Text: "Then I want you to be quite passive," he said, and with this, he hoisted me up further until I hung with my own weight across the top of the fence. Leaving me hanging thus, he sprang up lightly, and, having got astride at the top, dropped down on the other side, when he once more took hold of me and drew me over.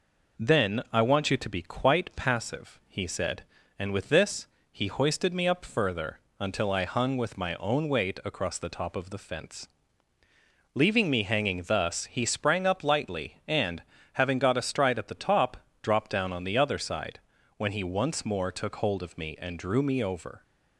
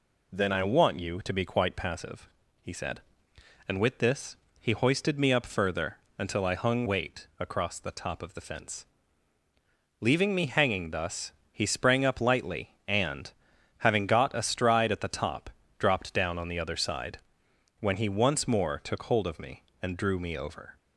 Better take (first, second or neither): first